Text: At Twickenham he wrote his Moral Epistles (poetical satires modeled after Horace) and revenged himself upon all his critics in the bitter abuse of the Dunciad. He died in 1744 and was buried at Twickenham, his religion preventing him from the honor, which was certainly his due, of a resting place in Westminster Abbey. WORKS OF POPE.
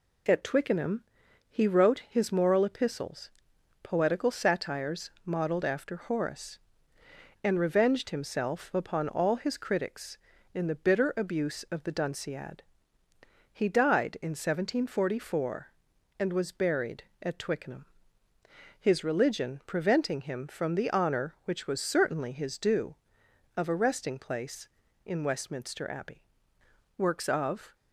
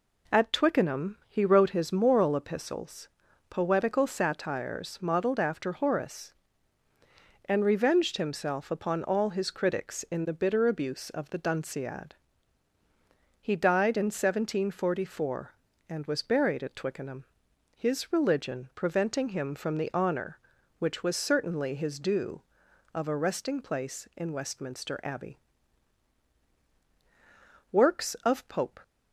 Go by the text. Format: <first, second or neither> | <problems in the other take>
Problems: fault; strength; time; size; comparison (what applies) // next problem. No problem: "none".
second | pauses between "Twickenham" and "he"; noticeable; at 1.0 s; 0.46 s long // pauses between "satires" and "modeled"; slight; at 5.0 s; 0.16 s long // stops before "POPE"; at 27.7 s